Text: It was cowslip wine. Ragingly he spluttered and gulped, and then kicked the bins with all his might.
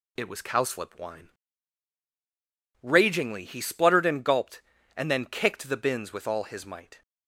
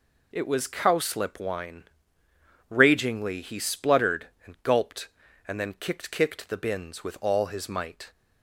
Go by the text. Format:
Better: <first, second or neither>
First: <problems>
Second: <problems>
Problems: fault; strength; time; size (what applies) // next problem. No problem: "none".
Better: first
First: none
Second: says "kicked" twice; at 6.1 s